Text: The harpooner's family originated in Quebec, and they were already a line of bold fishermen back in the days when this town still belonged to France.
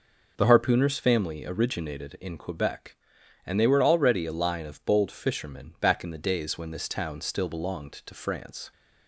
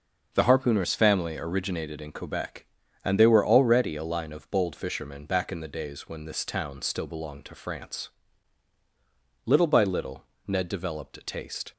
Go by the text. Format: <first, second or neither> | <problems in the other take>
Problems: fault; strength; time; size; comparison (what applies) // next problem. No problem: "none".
first | starts louder than the rest; noticeable; until 1.3 s; 6 dB // goes on to say "Little by little Ned developed a taste"; strong; from 9.4 s on; 2.2 s long